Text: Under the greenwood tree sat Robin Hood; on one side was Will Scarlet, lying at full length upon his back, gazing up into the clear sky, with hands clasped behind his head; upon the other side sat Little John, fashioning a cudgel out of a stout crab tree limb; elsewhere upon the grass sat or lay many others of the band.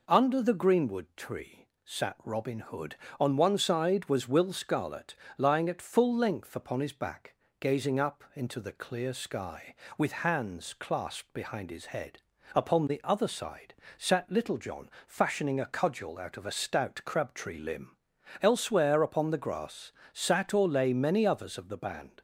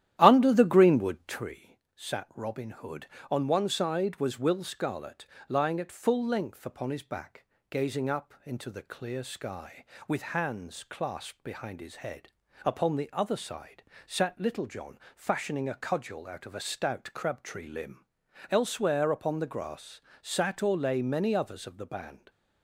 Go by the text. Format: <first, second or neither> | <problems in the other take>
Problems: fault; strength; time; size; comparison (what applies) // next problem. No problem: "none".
first | starts louder than the rest; strong; until 1.5 s; 12 dB // pauses between "tree" and "sat"; slight; at 1.7 s; 0.18 s long; slight in the first // pauses between "side" and "sat"; slight; at 13.8 s; 0.24 s long; slight in the first // pauses between "grass" and "sat"; slight; at 19.9 s; 0.22 s long; slight in the first